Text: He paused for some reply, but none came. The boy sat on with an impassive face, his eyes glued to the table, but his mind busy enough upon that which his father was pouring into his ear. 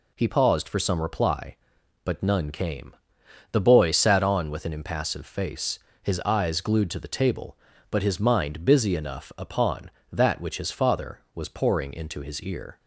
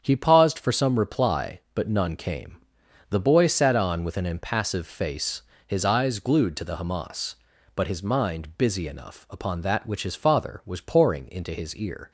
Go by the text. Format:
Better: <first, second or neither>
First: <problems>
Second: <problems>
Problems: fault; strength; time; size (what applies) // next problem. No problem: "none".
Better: first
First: none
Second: starts louder than the rest; strong; until 1.0 s; 8 dB // says "hamas" for "table"; at 6.7 s